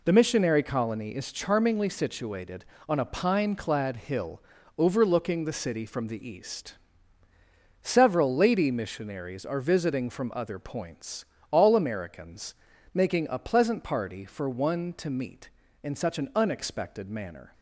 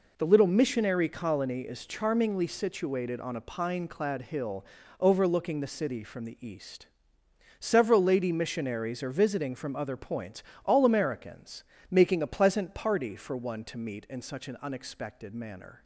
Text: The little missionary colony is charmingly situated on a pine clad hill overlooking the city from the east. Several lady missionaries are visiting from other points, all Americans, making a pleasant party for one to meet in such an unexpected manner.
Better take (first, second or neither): second